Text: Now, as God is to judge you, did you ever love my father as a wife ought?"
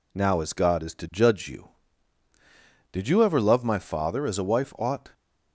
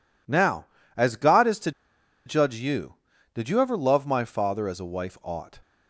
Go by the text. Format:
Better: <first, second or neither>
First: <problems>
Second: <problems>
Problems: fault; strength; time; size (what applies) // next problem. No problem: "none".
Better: first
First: none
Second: pauses between "to" and "judge"; noticeable; at 1.7 s; 0.55 s long